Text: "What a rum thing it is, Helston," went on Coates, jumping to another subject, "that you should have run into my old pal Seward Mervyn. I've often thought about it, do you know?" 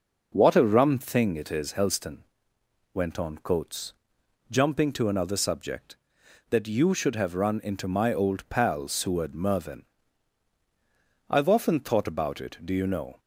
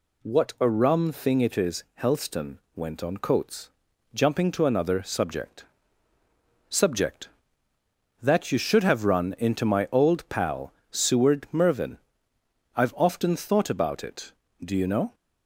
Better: first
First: none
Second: says "subject" twice; at 6.6 s // pauses between "pal" and "Seward"; slight; at 10.7 s; 0.16 s long

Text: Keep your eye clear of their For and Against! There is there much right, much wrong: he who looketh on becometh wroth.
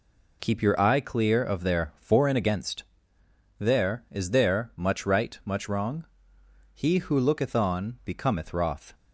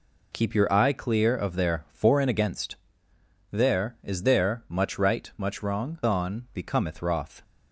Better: first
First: none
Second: skips "he who looketh"; at 6.0 s

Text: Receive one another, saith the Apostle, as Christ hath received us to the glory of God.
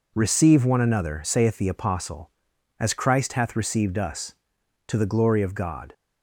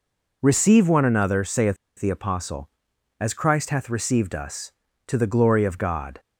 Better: first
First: none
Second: pauses between "saith" and "the"; slight; at 1.7 s; 0.23 s long

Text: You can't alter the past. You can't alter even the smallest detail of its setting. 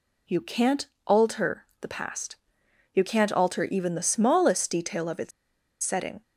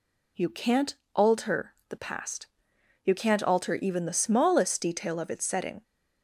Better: second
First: pauses between "can't" and "alter"; slight; at 0.8 s; 0.18 s long // pauses between "alter" and "the"; slight; at 1.6 s; 0.16 s long // pauses between "its" and "setting"; noticeable; at 5.3 s; 0.52 s long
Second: pauses between "can't" and "alter"; slight; at 0.9 s; 0.18 s long // pauses between "alter" and "the"; slight; at 1.7 s; 0.16 s long

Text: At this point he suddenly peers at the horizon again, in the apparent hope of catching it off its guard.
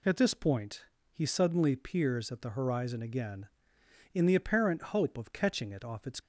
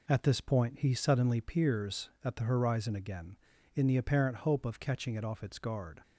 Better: second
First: pauses between "point" and "he"; slight; at 0.8 s; 0.28 s long // stops before "guard"; at 6.1 s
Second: none

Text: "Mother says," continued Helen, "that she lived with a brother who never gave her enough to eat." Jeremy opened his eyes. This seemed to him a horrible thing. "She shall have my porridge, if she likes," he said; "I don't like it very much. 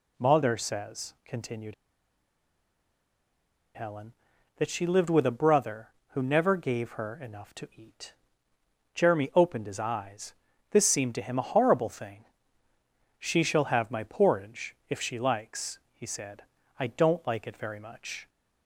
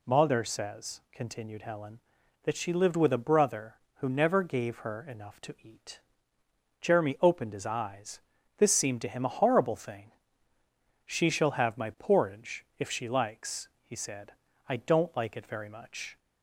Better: second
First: pauses between "continued" and "Helen"; strong; at 1.7 s; 2.0 s long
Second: none

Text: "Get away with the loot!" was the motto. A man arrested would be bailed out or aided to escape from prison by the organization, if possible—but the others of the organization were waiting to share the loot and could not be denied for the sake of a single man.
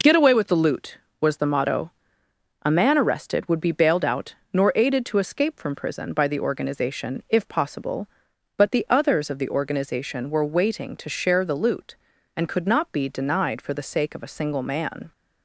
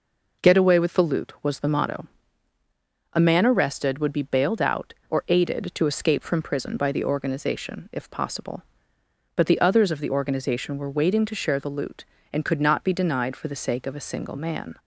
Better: second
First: says "nor" for "or"; at 4.5 s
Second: none

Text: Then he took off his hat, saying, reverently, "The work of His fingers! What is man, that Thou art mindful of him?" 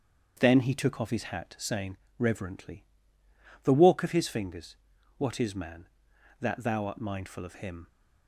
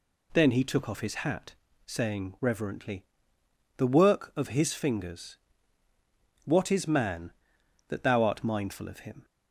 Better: second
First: starts louder than the rest; strong; until 1.4 s; 7.5 dB // says "walk" for "work"; at 3.7 s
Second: none

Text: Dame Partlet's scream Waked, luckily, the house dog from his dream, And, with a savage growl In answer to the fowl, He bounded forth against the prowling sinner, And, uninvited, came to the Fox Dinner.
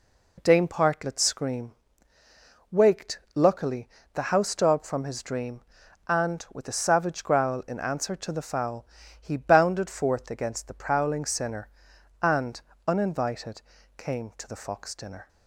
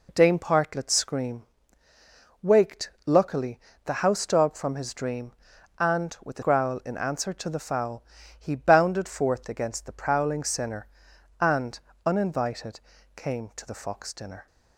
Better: first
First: pauses between "scream" and "Waked"; noticeable; at 1.7 s; 0.98 s long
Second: pauses between "scream" and "Waked"; noticeable; at 1.4 s; 0.98 s long // skips "savage"; at 6.4 s

